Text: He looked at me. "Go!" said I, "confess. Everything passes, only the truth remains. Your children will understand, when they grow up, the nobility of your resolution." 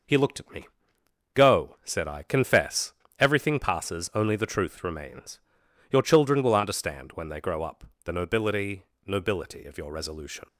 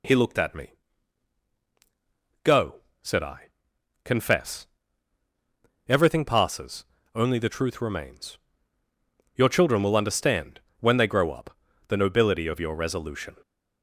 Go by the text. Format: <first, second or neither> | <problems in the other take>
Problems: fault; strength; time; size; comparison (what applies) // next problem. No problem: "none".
second | says "nobility" twice; at 9.0 s